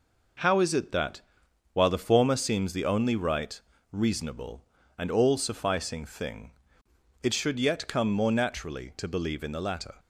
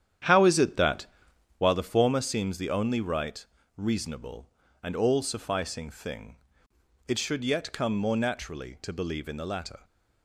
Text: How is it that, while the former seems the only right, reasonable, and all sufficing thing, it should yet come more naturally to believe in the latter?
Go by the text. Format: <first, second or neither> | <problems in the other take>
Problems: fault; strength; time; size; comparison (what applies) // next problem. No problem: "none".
first | starts louder than the rest; strong; until 1.7 s; 10 dB